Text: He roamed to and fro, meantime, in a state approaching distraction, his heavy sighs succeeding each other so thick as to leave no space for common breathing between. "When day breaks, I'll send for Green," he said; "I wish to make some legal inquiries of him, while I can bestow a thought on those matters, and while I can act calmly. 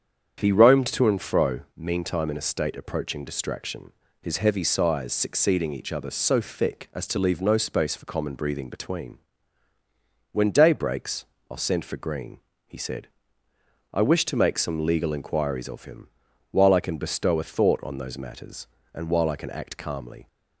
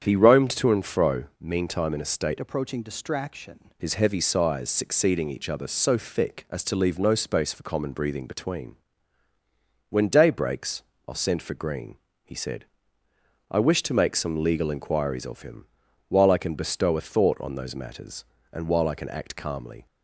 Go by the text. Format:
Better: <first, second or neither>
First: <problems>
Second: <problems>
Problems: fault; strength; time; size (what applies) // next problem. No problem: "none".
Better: first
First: starts louder than the rest; strong; until 1.4 s; 8 dB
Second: starts louder than the rest; strong; until 1.0 s; 8 dB // changes voice from "approaching" to "distraction"; from 2.4 to 3.7 s; 1.3 s long